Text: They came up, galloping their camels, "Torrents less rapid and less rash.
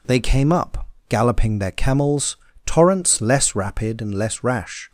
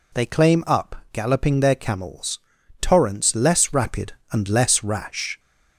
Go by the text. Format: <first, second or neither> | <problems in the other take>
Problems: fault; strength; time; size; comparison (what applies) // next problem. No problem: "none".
first | says "claim" for "came"; at 0.2 s